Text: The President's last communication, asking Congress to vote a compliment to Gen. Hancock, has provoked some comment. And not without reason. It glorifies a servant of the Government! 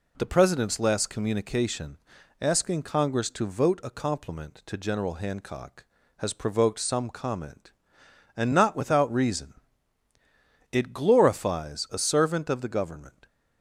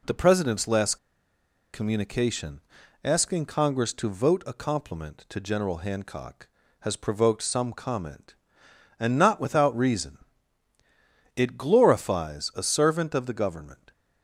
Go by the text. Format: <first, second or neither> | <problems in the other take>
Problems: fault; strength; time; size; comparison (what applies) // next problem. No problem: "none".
first | pauses between "last" and "communication"; noticeable; at 0.9 s; 0.77 s long